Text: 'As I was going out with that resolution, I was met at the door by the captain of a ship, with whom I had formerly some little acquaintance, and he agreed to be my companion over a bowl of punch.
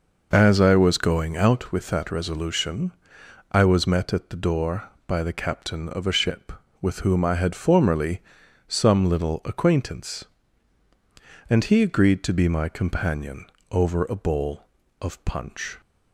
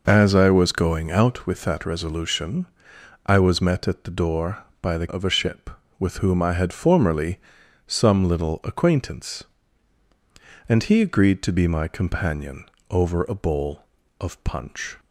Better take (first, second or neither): first